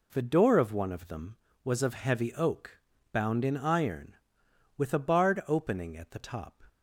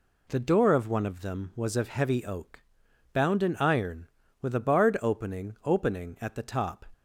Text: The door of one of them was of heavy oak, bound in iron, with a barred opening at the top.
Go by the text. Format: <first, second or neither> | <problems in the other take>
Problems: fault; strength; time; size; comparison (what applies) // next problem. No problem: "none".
first | says "opening" twice; at 5.6 s